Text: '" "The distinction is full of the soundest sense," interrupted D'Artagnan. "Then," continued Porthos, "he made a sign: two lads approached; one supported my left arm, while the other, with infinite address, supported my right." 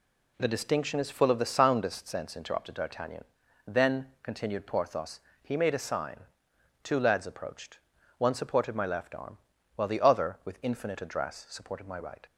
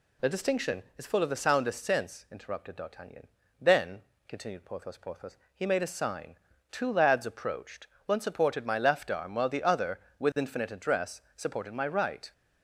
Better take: first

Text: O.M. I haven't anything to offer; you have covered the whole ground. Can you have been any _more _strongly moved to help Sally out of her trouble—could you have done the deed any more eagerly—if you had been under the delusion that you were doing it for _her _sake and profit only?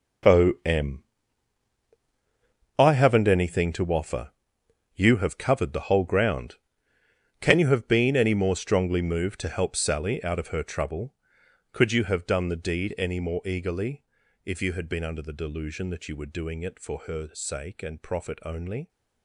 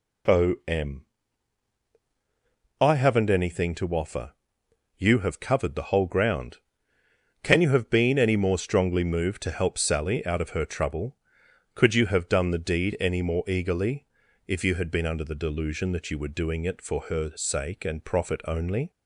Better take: second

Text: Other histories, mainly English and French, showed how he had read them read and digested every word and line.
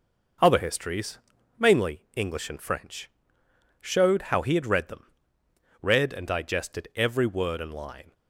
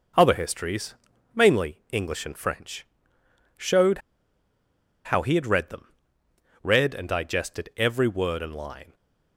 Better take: first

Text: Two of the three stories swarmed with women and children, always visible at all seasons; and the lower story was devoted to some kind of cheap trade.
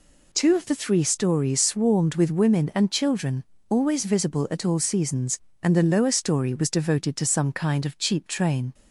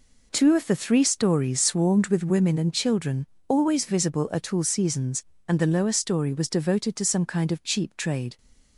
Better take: second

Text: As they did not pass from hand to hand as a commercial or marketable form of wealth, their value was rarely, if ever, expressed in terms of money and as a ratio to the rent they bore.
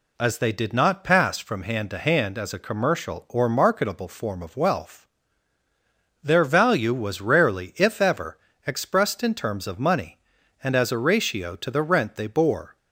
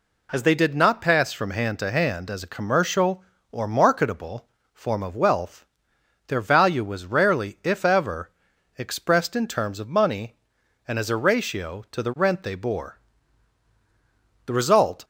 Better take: first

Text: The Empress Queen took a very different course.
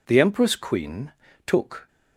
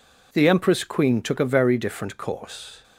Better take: second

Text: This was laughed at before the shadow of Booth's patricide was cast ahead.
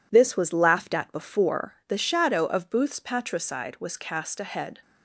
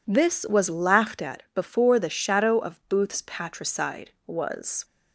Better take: first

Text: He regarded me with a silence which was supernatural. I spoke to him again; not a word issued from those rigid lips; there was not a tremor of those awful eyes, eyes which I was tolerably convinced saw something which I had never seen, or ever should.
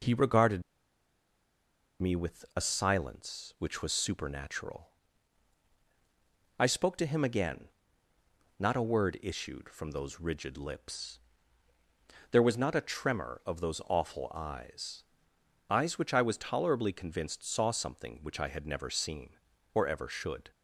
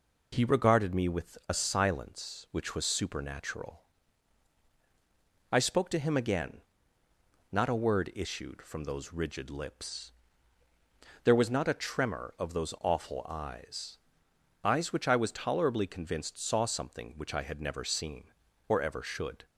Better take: second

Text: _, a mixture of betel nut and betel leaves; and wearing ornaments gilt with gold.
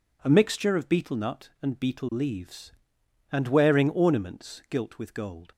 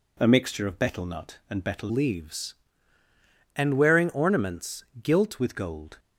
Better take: first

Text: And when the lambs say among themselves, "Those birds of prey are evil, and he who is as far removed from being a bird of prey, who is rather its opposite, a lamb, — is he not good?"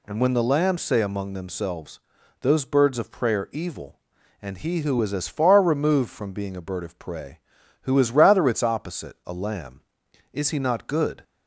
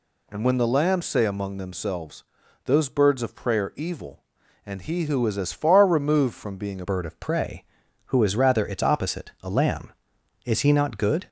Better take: first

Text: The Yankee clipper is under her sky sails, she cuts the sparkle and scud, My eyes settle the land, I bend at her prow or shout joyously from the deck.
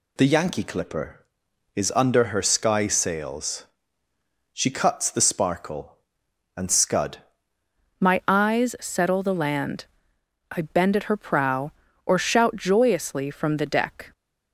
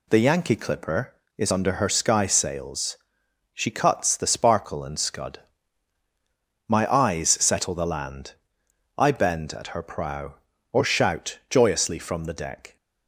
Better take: second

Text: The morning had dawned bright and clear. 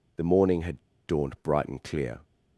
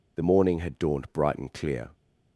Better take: second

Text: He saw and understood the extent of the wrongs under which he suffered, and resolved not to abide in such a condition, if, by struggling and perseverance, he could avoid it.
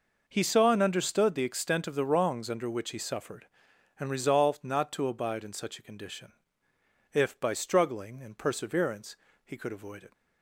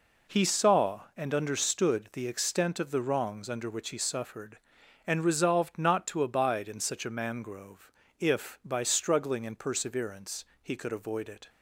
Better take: first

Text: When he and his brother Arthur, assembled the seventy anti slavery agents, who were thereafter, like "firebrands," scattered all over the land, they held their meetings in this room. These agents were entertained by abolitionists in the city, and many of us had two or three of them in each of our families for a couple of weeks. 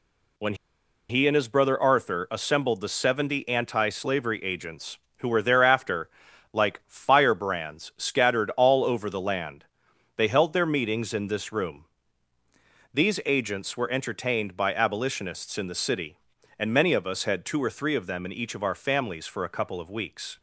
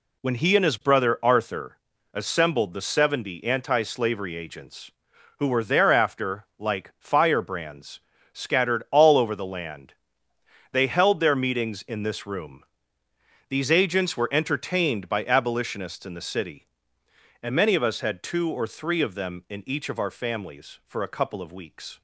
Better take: second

